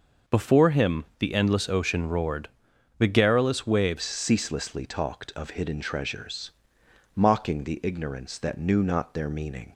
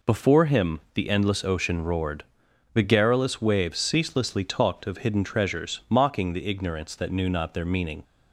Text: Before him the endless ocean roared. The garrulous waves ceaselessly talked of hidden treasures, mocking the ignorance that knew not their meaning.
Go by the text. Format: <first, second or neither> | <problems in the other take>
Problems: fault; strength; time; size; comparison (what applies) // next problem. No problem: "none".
second | pauses between "him" and "the"; slight; at 1.0 s; 0.16 s long; slight in the second // changes voice at "ceaselessly"; from 4.0 s on; 5.7 s long